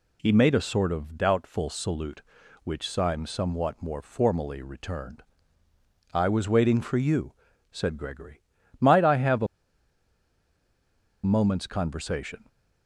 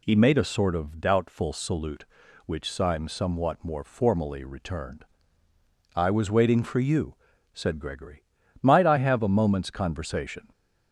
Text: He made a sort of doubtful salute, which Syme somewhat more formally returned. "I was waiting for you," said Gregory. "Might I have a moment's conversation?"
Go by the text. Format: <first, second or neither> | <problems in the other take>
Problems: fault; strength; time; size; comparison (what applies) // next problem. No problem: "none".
second | pauses between "a" and "moment's"; strong; at 9.4 s; 1.7 s long